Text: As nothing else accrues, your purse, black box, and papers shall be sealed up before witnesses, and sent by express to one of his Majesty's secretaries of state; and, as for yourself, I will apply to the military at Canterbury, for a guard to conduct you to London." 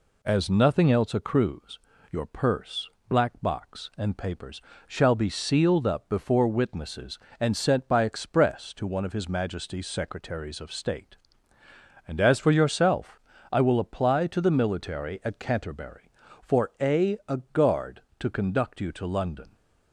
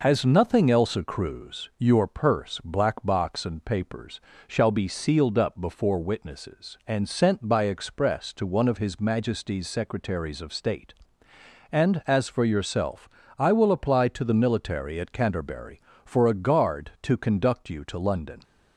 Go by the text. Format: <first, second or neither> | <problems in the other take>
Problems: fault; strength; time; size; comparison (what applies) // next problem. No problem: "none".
second | pauses between "papers" and "shall"; slight; at 4.5 s; 0.26 s long; slight in the second // says "a" twice; at 17.2 s